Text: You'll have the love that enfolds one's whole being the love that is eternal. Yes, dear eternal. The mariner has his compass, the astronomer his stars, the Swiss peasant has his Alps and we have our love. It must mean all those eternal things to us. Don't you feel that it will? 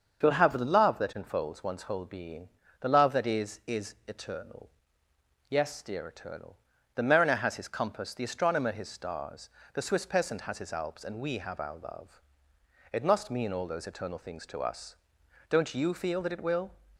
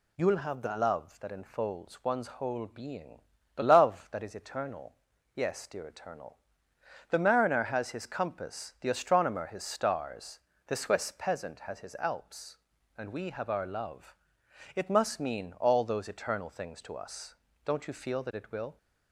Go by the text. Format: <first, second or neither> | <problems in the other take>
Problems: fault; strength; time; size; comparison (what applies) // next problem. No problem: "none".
second | starts louder than the rest; until 1.2 s; 6.5 dB // pauses between "being" and "the"; slight; at 2.4 s; 0.32 s long; slight in the second // says "is" twice; at 3.6 s